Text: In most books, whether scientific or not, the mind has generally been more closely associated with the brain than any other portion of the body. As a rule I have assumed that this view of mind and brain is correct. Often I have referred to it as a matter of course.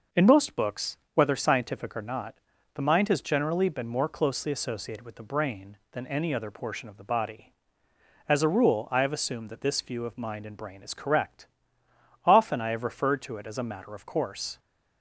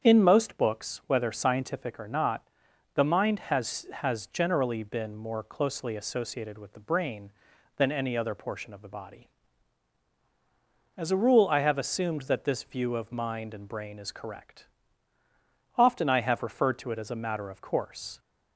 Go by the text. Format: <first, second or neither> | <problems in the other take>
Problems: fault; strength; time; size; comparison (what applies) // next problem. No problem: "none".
first | starts louder than the rest; strong; until 1.0 s; 8 dB // says "has" twice; at 3.9 s